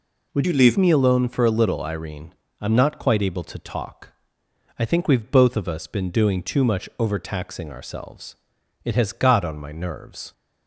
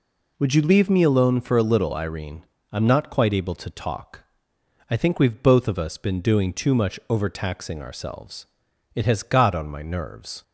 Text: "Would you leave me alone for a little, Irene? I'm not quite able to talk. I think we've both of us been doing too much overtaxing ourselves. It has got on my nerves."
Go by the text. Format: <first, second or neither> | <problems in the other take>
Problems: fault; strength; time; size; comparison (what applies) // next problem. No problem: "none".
second | changes voice from "you" to "leave"; from 0.4 to 0.7 s; 0.3 s long